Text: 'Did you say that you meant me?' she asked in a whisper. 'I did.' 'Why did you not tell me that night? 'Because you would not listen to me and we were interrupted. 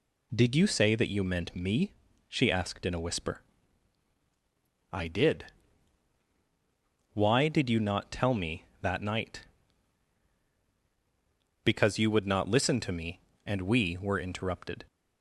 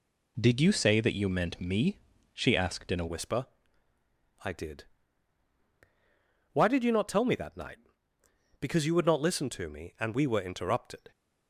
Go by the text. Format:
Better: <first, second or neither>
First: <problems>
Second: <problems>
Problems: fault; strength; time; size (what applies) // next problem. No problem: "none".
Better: first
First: none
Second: changes voice at "whisper"; from 3.0 s on; 8.1 s long